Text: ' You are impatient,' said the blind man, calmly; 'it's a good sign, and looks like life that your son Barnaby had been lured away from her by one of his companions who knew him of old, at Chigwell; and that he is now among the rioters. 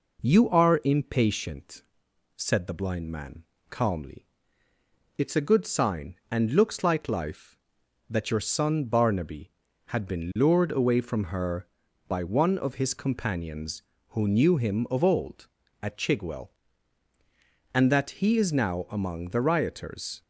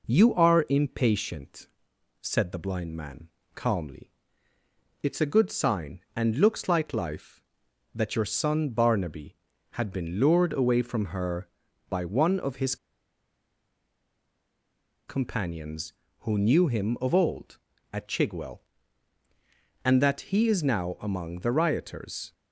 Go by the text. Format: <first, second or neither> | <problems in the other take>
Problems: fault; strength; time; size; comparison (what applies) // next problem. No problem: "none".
first | pauses between "his" and "companions"; strong; at 12.7 s; 2.3 s long